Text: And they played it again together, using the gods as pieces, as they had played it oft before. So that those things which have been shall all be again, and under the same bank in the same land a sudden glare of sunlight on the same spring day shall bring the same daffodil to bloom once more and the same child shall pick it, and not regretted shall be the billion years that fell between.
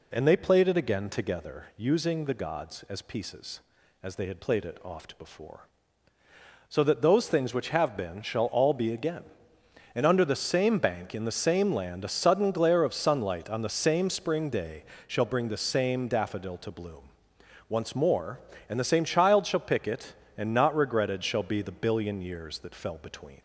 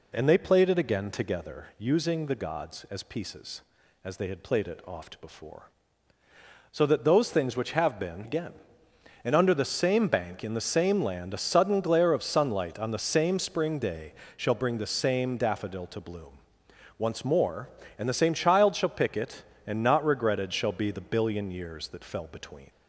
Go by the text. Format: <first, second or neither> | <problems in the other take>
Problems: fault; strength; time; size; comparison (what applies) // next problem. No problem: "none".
first | skips "shall all be"; at 8.2 s // pauses between "day" and "shall"; slight; at 14.1 s; 0.24 s long; slight in the first // pauses between "bloom" and "once"; noticeable; at 16.3 s; 0.60 s long; noticeable in the first